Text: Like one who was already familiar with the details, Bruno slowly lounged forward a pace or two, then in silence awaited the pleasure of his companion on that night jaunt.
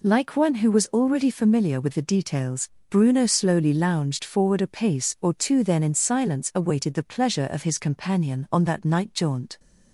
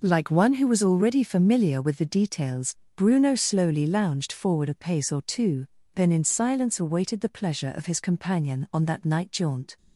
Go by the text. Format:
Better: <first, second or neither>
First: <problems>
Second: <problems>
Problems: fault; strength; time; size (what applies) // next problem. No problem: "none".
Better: neither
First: none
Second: none